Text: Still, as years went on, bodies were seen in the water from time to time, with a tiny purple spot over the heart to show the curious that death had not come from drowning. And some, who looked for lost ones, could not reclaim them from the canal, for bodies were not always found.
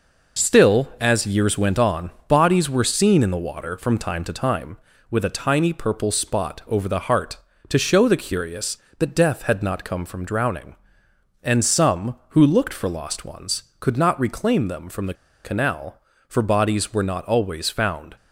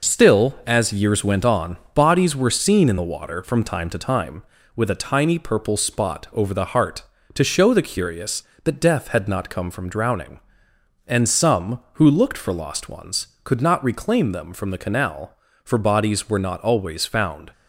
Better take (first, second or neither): second